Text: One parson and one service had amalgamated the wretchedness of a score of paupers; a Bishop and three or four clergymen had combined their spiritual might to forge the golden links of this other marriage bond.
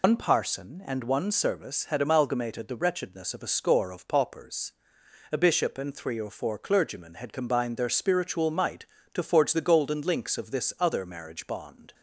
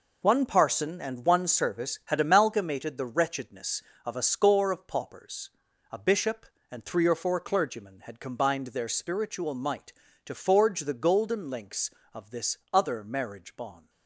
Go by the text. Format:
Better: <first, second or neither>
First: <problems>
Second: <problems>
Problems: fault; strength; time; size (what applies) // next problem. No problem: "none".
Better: second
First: loses the start of "One"; at 0.0 s; 105 ms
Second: none